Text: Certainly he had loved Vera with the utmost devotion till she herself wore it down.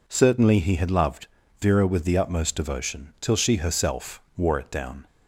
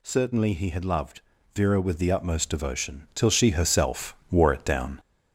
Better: first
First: pauses between "loved" and "Vera"; slight; at 1.2 s; 0.34 s long // pauses between "herself" and "wore"; slight; at 4.2 s; 0.16 s long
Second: gets louder; slight; throughout; 3 dB // pauses between "loved" and "Vera"; slight; at 1.2 s; 0.34 s long // pauses between "herself" and "wore"; slight; at 4.1 s; 0.16 s long

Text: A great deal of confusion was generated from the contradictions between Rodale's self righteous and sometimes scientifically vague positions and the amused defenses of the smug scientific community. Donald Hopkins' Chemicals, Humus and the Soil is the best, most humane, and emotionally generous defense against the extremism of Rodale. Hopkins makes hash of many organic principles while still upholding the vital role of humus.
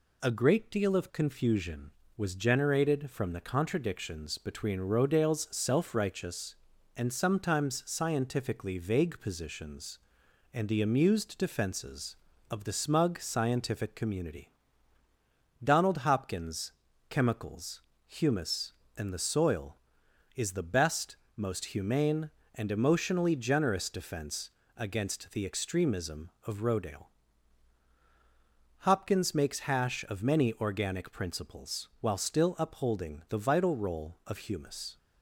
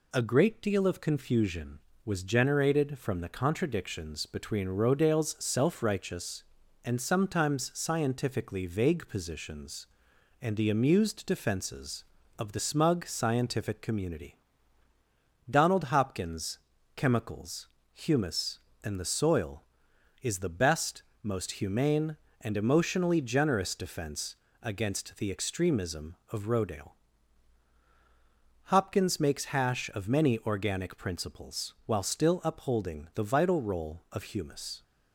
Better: neither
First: pauses between "Hopkins" and "Chemicals"; at 16.7 s; 0.38 s long // pauses between "defense" and "against"; slight; at 24.5 s; 0.26 s long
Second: pauses between "Hopkins" and "Chemicals"; at 16.5 s; 0.38 s long // pauses between "defense" and "against"; slight; at 24.3 s; 0.26 s long

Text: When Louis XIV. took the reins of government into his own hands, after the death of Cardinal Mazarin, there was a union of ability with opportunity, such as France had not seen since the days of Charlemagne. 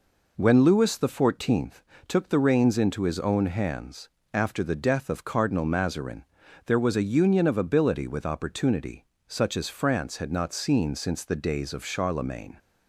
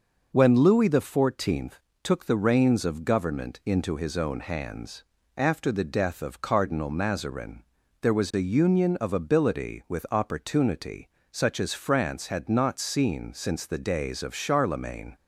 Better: second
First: skips "of government"; at 2.7 s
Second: none

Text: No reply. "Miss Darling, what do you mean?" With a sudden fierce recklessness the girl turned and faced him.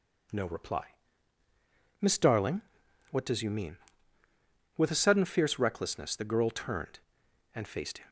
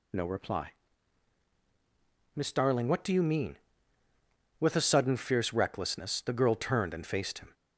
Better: second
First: says "does" for "do"; at 3.2 s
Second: none

